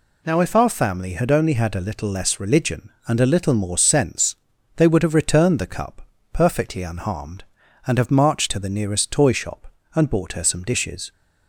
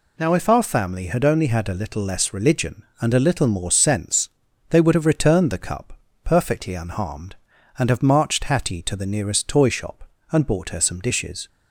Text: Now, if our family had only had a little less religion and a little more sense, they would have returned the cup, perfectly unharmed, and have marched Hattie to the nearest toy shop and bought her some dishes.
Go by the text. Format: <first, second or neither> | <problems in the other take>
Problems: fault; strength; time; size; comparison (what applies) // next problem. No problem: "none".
second | skips "Hattie"; at 8.4 s